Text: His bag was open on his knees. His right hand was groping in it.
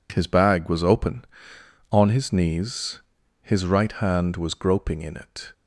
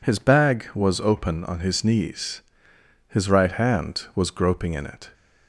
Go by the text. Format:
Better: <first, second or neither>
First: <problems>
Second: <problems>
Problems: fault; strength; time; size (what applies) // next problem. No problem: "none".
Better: neither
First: none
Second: none